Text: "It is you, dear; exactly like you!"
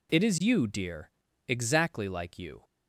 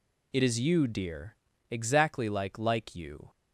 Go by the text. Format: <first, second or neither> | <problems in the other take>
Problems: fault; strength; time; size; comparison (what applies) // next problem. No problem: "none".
first | says "like" twice; at 2.5 s